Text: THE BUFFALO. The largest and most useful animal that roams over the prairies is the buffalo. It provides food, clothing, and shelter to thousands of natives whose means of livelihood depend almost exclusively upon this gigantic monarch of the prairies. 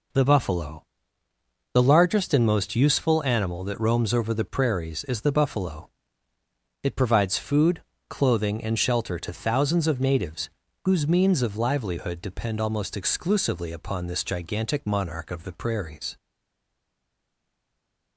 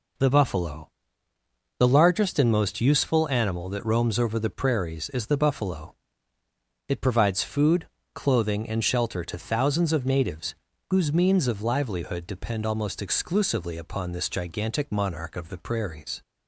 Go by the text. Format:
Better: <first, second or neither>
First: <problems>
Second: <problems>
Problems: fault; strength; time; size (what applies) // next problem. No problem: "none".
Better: second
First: pauses between "natives" and "whose"; slight; at 10.5 s; 0.34 s long // stays silent after the last word; noticeable; from 16.1 s on; 2.0 s long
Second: pauses between "natives" and "whose"; slight; at 10.5 s; 0.34 s long